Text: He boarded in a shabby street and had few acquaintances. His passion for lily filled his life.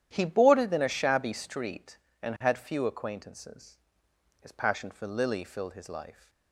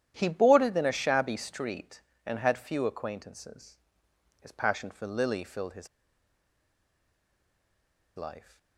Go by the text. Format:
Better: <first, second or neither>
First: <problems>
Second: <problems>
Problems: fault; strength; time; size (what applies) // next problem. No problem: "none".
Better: first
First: starts louder than the rest; strong; until 1.1 s; 10.5 dB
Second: starts louder than the rest; strong; until 1.1 s; 10.5 dB // pauses between "his" and "life"; strong; at 5.8 s; 2.3 s long